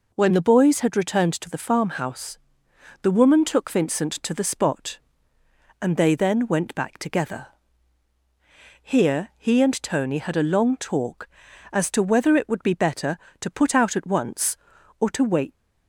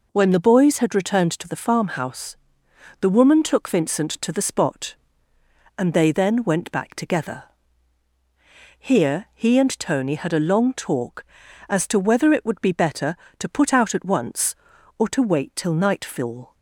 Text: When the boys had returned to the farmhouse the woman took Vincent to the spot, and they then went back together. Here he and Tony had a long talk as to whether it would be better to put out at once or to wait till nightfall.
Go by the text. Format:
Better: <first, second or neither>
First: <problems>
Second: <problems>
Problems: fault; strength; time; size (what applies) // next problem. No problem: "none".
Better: second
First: pauses between "farmhouse" and "the"; noticeable; at 2.3 s; 0.66 s long // stops before "till nightfall"; at 15.5 s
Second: pauses between "farmhouse" and "the"; noticeable; at 2.3 s; 0.66 s long